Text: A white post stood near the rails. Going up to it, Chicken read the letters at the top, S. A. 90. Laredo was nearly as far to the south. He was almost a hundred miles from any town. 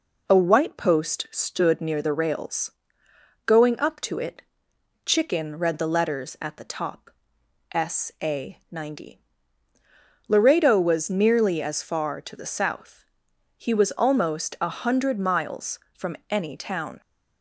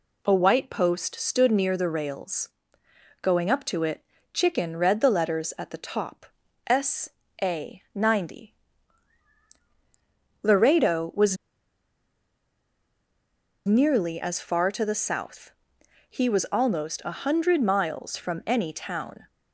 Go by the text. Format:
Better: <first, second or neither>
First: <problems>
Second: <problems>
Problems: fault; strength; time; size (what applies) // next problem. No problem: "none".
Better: first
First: none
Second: pauses between "was" and "nearly"; strong; at 11.3 s; 2.3 s long